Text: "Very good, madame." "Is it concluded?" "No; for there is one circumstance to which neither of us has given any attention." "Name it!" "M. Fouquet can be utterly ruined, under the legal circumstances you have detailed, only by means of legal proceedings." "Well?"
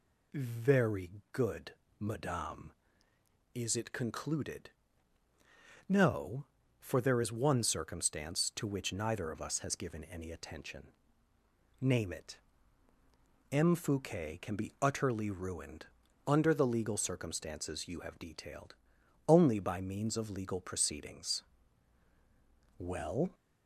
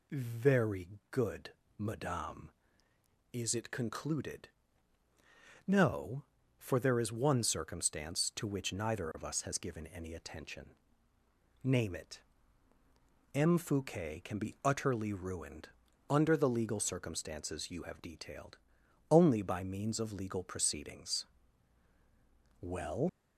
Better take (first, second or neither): first